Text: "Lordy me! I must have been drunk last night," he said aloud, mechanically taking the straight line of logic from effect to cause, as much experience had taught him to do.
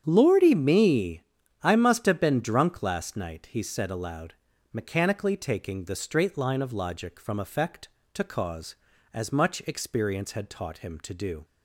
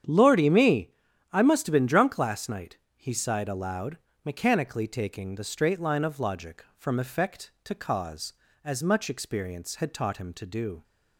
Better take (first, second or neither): first